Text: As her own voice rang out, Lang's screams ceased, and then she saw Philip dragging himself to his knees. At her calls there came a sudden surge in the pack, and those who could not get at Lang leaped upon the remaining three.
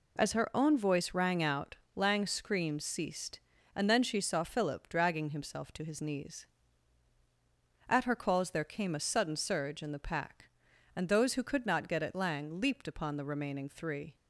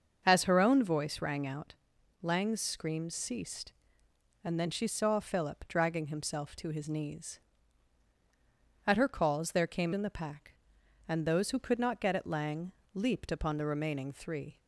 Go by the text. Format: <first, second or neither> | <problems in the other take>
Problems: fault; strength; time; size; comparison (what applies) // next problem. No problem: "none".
first | starts louder than the rest; until 1.2 s; 6.5 dB // skips "a sudden surge"; at 9.9 s // pauses between "Lang" and "leaped"; slight; at 12.7 s; 0.22 s long